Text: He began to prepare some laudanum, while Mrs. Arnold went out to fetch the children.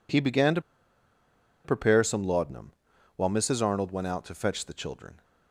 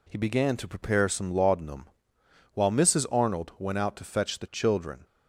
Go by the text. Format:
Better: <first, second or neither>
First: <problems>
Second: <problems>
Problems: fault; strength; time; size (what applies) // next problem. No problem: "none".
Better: second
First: pauses between "to" and "prepare"; at 0.6 s; 1.0 s long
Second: none